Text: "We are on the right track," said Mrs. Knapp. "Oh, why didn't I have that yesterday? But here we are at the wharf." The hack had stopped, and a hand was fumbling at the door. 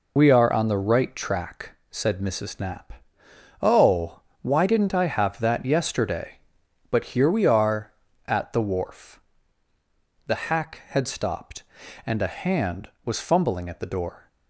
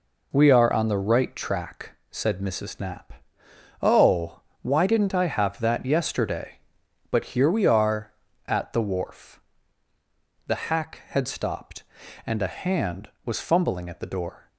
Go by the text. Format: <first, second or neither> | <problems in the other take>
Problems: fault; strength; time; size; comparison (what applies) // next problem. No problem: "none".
second | loses the start of "We"; at 0.1 s; 40 ms